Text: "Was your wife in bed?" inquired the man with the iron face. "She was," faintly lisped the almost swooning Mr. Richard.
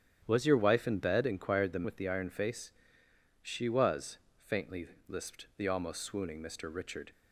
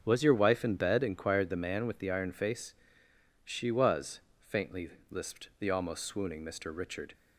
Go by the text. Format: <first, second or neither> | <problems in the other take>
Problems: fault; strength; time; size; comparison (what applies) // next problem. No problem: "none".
second | starts louder than the rest; strong; until 1.2 s; 10 dB; also in the second // skips "man"; at 1.8 s // pauses between "faintly" and "lisped"; slight; at 4.8 s; 0.22 s long; slight in the second